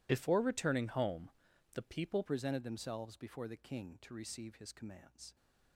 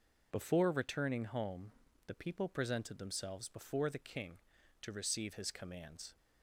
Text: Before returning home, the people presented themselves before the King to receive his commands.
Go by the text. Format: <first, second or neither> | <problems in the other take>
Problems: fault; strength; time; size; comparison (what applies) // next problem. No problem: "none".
second | changes voice at "presented"; from 2.2 s on; 3.1 s long